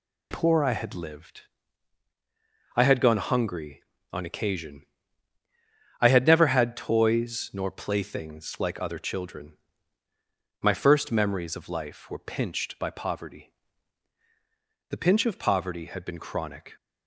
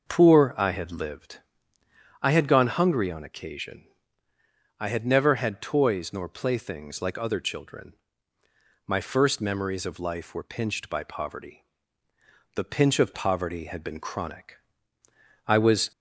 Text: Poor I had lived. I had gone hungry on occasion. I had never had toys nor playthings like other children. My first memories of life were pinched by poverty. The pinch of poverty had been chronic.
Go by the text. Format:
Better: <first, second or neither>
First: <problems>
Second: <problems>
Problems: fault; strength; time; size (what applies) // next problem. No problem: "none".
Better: first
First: none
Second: goes on to say "I was"; slight; from 15.4 s on; 0.46 s long